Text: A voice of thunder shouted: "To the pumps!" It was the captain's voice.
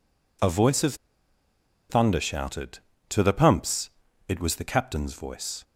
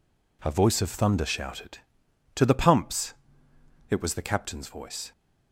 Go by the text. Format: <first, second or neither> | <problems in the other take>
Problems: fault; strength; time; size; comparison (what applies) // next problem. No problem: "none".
second | pauses between "of" and "thunder"; noticeable; at 0.9 s; 0.94 s long